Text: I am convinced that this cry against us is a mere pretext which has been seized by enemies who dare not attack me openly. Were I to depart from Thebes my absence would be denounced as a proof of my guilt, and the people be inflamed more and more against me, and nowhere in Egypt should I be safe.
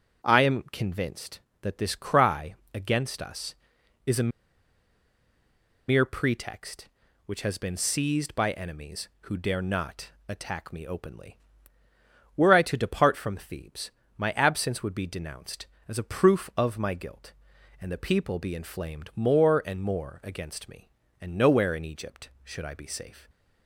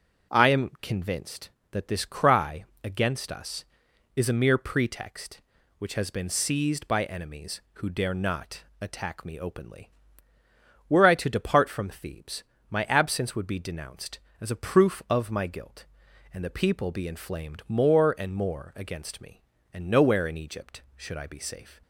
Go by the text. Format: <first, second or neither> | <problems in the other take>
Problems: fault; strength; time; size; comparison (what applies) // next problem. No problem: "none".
second | starts louder than the rest; until 1.3 s; 6.5 dB; also in the second // pauses between "cry" and "against"; slight; at 2.5 s; 0.20 s long; slight in the second // pauses between "a" and "mere"; strong; at 4.3 s; 1.6 s long // pauses between "not" and "attack"; slight; at 10.1 s; 0.16 s long; slight in the second // pauses between "Thebes" and "my"; slight; at 13.9 s; 0.26 s long; slight in the second